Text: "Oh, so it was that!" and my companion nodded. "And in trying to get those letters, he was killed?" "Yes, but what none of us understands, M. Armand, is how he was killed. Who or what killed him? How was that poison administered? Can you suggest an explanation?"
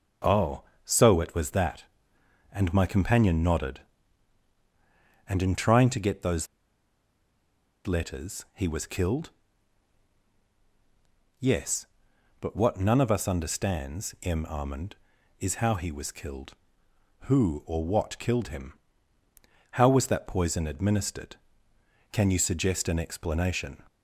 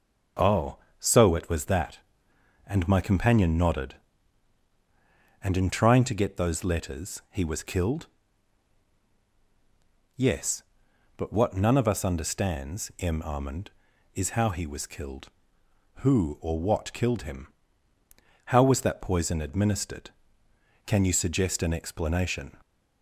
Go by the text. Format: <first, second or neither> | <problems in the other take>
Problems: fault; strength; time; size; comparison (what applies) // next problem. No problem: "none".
second | pauses between "those" and "letters"; strong; at 6.4 s; 1.4 s long